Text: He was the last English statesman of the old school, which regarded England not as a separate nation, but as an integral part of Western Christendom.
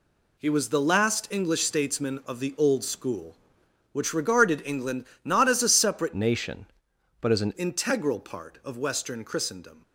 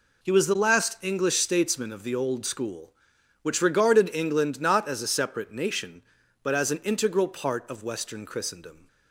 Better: second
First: pauses between "England" and "not"; slight; at 5.0 s; 0.20 s long // changes voice from "nation" to "an"; from 6.1 to 7.5 s; 1.4 s long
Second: none

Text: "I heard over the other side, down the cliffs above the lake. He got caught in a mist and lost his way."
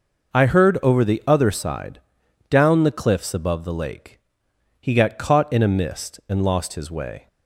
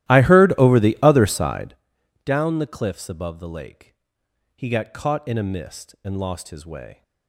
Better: first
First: none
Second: starts louder than the rest; strong; until 1.8 s; 14.5 dB

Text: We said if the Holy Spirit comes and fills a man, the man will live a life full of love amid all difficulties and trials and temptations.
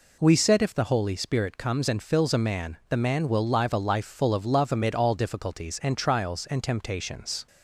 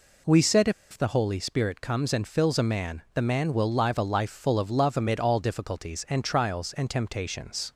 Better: first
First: none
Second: pauses between "said" and "if"; slight; at 0.6 s; 0.20 s long

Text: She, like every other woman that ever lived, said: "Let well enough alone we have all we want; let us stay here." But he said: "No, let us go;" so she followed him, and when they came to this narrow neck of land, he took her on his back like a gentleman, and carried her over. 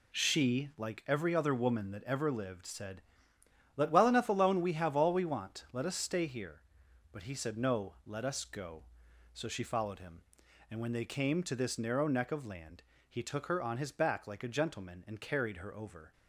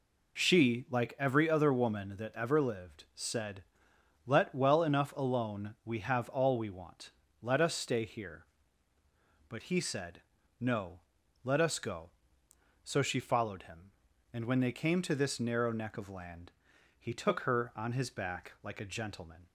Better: first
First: none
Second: stops before "and carried her over"; at 19.4 s

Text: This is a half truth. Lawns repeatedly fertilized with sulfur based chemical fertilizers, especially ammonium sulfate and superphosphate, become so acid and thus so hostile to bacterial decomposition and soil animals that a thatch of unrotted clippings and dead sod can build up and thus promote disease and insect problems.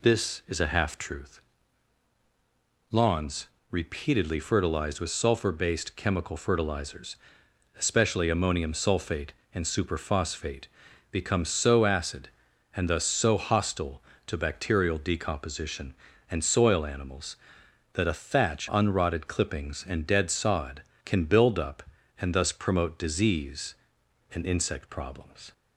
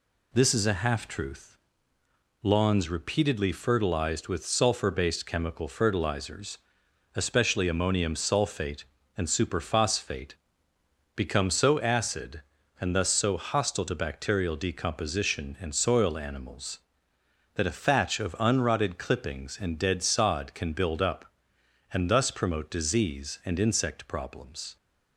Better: second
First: pauses between "Lawns" and "repeatedly"; slight; at 3.4 s; 0.22 s long // skips "of"; at 18.6 s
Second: none

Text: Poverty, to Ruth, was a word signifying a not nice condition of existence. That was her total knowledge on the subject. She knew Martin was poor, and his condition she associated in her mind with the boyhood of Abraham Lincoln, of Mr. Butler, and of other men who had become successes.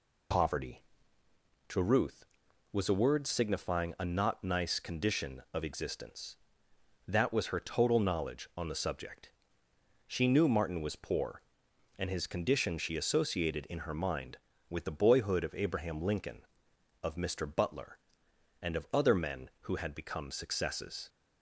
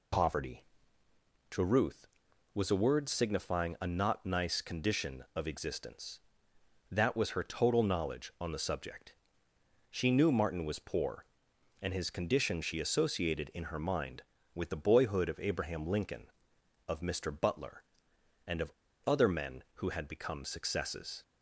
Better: first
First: none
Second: pauses between "of" and "other"; slight; at 18.7 s; 0.34 s long

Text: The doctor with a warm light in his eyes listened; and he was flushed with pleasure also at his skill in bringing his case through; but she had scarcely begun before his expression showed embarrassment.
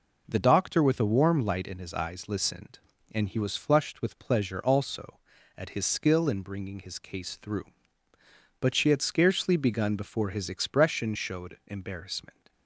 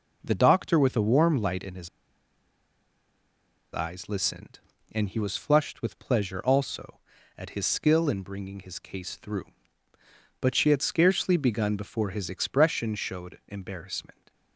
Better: first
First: none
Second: pauses between "his" and "eyes"; strong; at 1.8 s; 1.8 s long

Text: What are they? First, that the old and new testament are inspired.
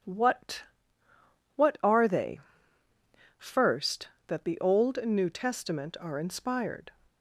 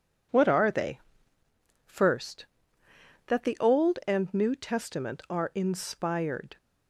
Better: second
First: says "What" twice; at 1.5 s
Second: none

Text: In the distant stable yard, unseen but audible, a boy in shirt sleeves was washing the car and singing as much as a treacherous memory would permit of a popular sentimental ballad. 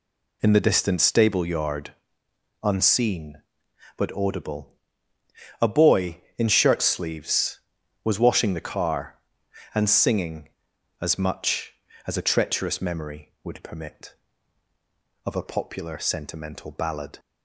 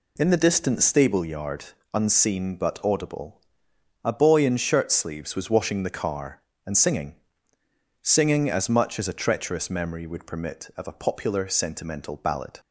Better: first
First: none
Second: says "singing" twice; at 8.0 s

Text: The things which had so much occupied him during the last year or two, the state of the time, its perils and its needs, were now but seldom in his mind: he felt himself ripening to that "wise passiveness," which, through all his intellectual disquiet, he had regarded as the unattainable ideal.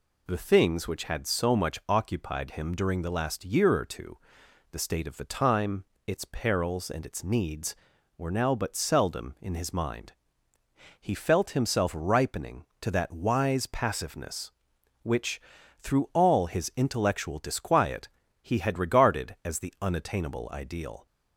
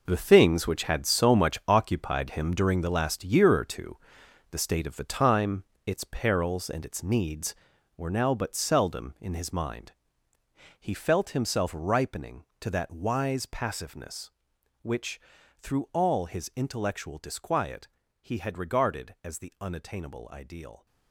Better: first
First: none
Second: gets quieter; strong; throughout; 12.5 dB

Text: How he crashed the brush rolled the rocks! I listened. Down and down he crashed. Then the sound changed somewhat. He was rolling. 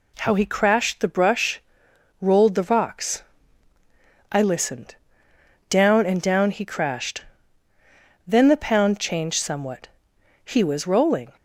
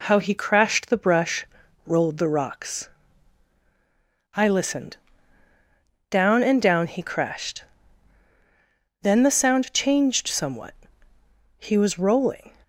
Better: second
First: pauses between "brush" and "rolled"; noticeable; at 1.6 s; 0.60 s long // says "pound" for "sound"; at 8.5 s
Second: pauses between "brush" and "rolled"; at 1.4 s; 0.40 s long

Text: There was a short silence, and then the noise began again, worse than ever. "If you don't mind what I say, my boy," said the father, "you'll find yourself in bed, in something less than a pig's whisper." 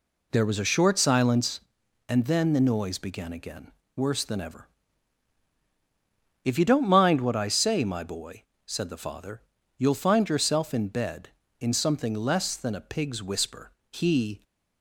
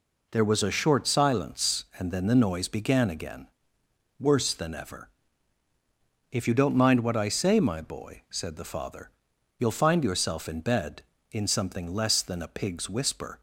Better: second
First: goes on to say "He"; from 13.9 s on; 0.52 s long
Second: none

